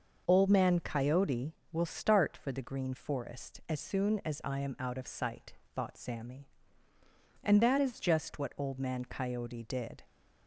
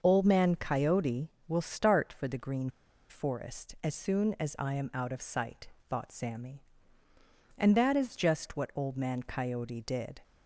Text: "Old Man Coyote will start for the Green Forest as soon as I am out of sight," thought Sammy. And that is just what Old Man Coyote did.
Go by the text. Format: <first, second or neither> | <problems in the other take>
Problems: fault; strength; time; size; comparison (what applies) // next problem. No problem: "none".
first | starts louder than the rest; noticeable; until 1.0 s; 6 dB; noticeable in the first // pauses between "Green" and "Forest"; at 2.6 s; 0.40 s long